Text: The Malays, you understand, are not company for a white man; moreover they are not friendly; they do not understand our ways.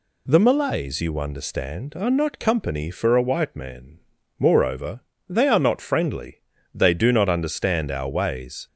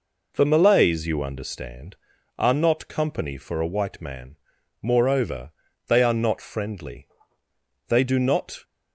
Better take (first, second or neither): first